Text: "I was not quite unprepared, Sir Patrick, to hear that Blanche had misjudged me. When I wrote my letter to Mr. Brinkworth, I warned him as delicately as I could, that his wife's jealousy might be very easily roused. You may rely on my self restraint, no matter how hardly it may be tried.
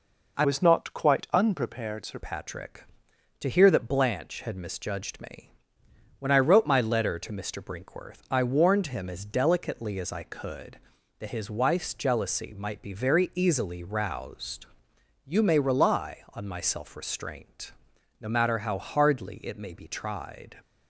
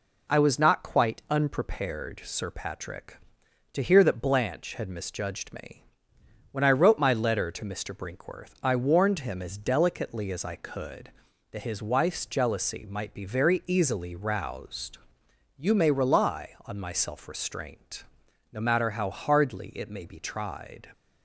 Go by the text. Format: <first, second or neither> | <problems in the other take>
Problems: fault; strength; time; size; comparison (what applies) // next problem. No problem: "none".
second | changes voice from "was" to "Sir"; from 0.4 to 2.1 s; 1.7 s long